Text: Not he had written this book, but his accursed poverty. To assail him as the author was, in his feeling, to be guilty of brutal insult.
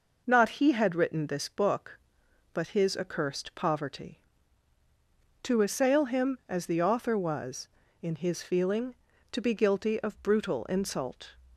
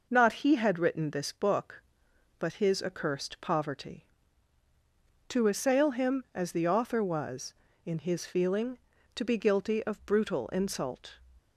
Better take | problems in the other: neither | none

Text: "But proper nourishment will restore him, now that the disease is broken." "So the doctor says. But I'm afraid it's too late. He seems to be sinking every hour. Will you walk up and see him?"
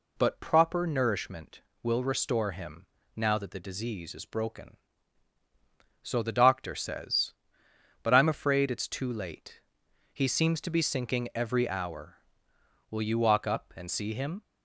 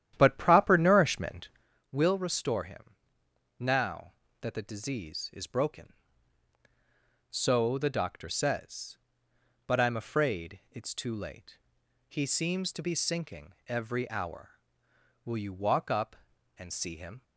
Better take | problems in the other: first | starts louder than the rest; strong; until 1.7 s; 11 dB

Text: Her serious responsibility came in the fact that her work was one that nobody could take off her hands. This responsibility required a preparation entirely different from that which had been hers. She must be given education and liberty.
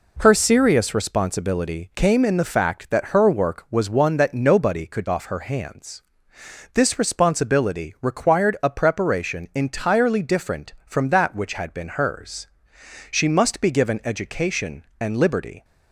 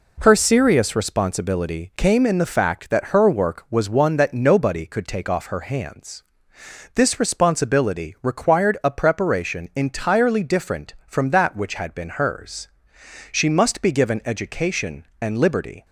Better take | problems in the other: second | skips "take"; at 5.0 s

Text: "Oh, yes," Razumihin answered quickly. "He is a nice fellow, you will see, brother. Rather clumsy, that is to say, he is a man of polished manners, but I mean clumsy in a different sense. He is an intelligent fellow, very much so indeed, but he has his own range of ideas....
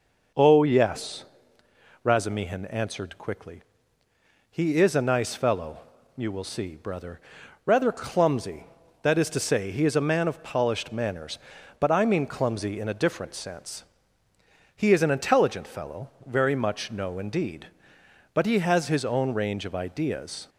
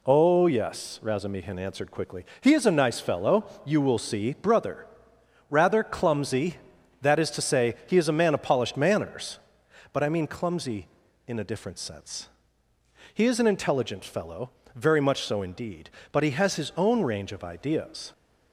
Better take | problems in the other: second | says "no" for "so"; at 16.9 s

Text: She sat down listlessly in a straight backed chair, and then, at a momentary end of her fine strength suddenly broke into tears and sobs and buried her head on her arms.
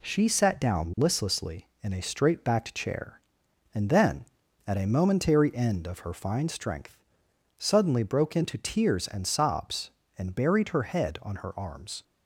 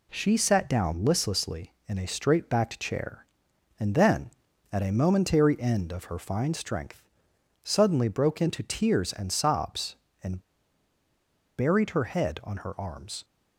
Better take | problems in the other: first | pauses between "strength" and "suddenly"; noticeable; at 7.0 s; 0.56 s long; noticeable in the first // pauses between "and" and "buried"; at 10.4 s; 1.1 s long

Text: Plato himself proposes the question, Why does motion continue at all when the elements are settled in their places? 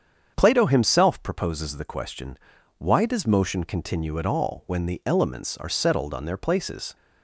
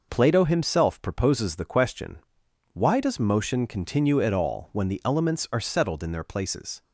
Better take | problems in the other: second | starts louder than the rest; strong; until 1.3 s; 8 dB // says "on" for "in"; at 6.1 s

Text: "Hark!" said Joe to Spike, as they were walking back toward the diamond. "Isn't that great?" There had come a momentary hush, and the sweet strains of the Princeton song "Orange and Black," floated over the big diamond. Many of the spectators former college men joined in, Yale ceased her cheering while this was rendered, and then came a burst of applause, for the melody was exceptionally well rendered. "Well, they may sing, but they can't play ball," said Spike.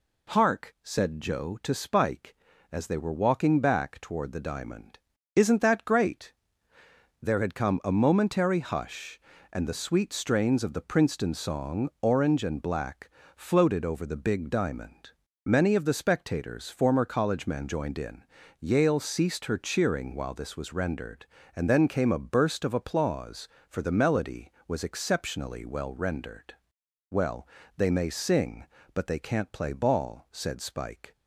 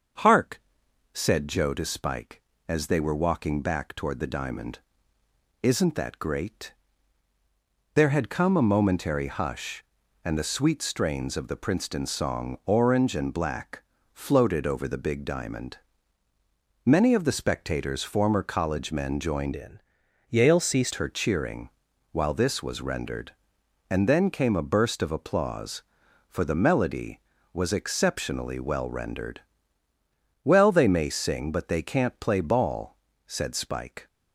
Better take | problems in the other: first | starts louder than the rest; until 1.7 s; 6.5 dB // changes voice from "in" to "ceased"; from 19.5 to 20.9 s; 1.4 s long // pauses between "cheering" and "while"; at 21.6 s; 0.42 s long

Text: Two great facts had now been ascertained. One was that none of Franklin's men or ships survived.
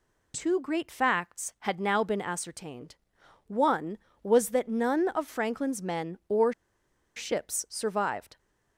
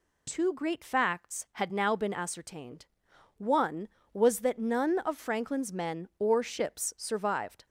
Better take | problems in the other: second | pauses between "or" and "ships"; noticeable; at 6.5 s; 0.64 s long

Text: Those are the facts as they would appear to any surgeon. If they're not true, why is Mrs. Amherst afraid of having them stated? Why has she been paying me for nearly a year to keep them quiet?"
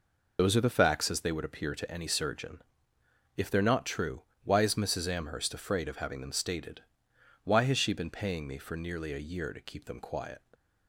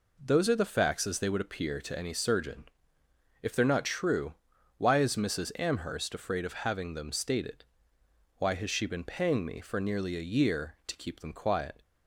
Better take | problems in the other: second | loses the start of "Those"; at 0.3 s; 55 ms

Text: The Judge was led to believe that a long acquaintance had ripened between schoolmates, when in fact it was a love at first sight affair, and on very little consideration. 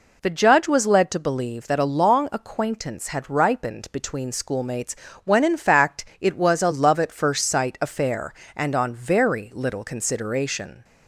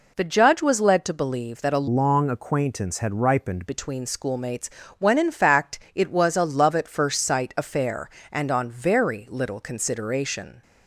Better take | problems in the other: first | changes voice from "long" to "ripened"; from 1.8 to 3.6 s; 1.8 s long

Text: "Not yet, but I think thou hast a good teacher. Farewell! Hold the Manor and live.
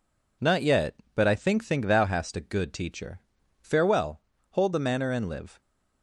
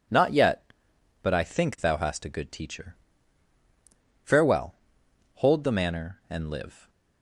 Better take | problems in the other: second | says "think" twice; at 1.6 s

